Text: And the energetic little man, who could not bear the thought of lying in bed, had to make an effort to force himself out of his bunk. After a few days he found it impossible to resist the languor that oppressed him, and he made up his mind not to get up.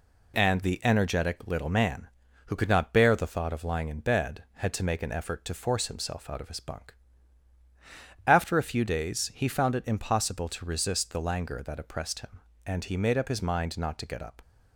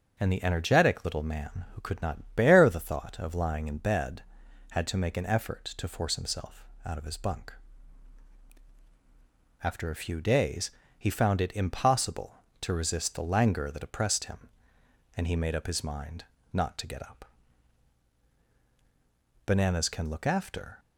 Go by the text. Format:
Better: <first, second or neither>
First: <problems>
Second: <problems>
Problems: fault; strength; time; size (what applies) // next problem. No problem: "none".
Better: first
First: none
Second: starts louder than the rest; until 1.1 s; 6.5 dB // pauses between "himself" and "out"; slight; at 6.6 s; 0.20 s long // pauses between "days" and "he"; slight; at 10.7 s; 0.26 s long // pauses between "mind" and "not"; slight; at 16.2 s; 0.28 s long // goes on to say "Bananas can look after"; from 19.4 s on; 1.3 s long